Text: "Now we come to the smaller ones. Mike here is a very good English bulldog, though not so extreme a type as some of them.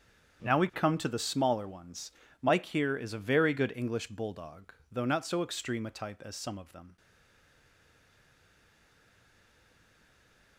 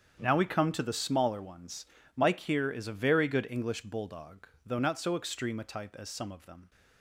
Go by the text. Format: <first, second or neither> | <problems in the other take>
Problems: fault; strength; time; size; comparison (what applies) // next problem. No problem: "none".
second | starts louder than the rest; strong; until 1.5 s; 8 dB; strong in the second // stays silent after the last word; strong; from 6.9 s on; 3.6 s long